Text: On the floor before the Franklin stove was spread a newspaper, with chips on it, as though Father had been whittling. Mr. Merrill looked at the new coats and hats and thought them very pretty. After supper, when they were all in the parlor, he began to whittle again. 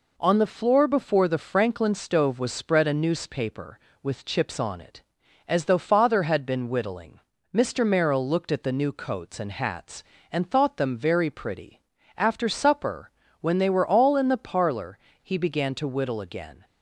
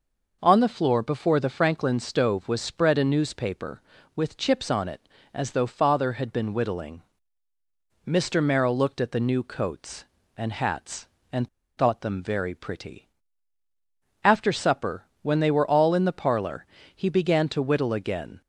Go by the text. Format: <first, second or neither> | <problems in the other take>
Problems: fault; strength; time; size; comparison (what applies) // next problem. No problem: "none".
first | pauses between "and" and "thought"; slight; at 11.4 s; 0.30 s long